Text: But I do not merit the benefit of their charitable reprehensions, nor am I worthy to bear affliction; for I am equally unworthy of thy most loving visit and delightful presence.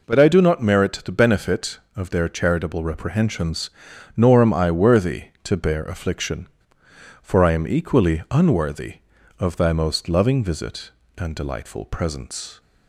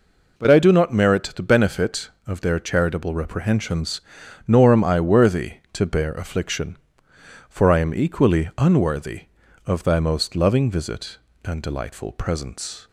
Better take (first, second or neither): neither